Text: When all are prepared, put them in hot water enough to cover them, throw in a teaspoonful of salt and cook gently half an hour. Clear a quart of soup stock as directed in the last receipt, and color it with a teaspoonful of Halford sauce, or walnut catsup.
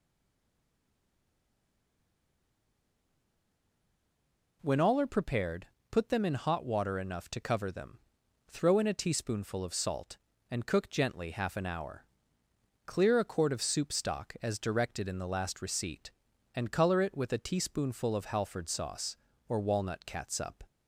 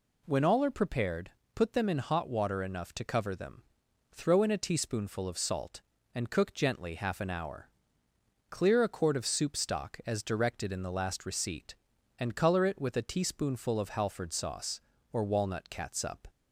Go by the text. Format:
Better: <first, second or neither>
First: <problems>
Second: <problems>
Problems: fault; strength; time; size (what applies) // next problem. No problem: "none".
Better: second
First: stays silent before the first word; strong; until 4.6 s; 4.6 s long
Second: none